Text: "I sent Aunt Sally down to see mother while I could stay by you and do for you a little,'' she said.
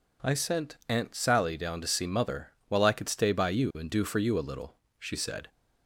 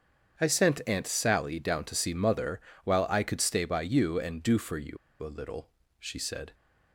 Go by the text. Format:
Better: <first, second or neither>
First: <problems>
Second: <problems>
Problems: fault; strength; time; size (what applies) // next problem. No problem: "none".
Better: first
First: pauses between "mother" and "while"; slight; at 2.5 s; 0.18 s long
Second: starts louder than the rest; strong; until 1.4 s; 7.5 dB // pauses between "mother" and "while"; slight; at 2.5 s; 0.24 s long // pauses between "you" and "a"; slight; at 4.9 s; 0.26 s long